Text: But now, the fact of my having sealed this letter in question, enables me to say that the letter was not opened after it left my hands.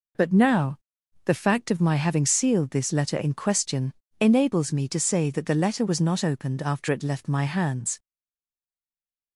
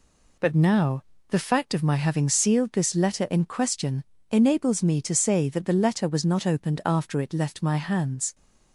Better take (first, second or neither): second